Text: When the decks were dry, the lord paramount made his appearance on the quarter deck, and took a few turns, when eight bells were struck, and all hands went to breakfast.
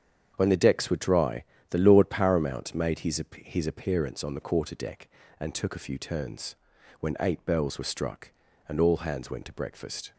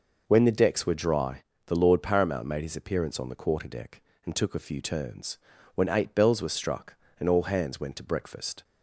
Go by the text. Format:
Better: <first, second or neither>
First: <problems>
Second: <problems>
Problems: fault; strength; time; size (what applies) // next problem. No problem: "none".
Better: second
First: starts louder than the rest; strong; until 1.3 s; 7.5 dB // says "his" twice; at 3.4 s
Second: none